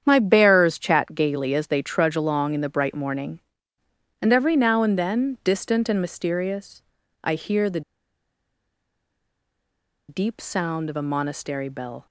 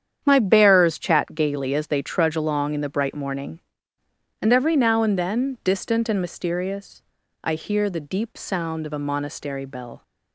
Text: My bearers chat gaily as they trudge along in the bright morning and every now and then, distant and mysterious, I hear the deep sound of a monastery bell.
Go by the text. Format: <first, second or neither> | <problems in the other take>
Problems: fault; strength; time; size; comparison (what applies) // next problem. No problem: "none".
second | starts louder than the rest; strong; until 1.0 s; 8.5 dB; strong in the second // pauses between "the" and "deep"; strong; at 7.8 s; 2.2 s long